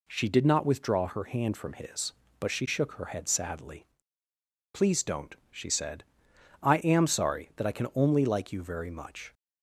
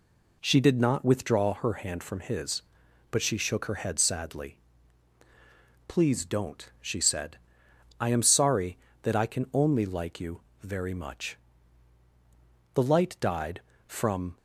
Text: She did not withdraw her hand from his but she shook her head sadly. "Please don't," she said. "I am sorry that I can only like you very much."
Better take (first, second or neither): first